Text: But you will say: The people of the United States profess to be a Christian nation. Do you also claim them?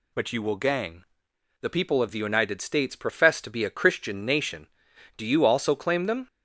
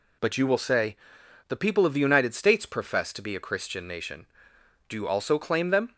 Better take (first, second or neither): second